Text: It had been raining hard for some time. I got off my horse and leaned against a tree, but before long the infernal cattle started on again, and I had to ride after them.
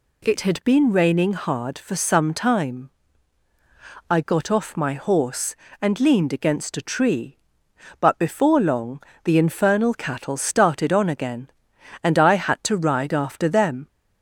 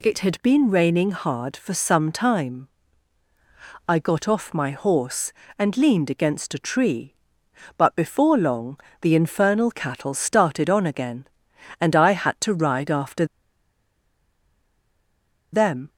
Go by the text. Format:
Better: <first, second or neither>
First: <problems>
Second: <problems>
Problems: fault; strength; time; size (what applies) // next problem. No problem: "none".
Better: first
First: pauses between "long" and "the"; slight; at 9.0 s; 0.22 s long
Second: pauses between "long" and "the"; slight; at 8.7 s; 0.22 s long // pauses between "after" and "them"; strong; at 13.2 s; 2.2 s long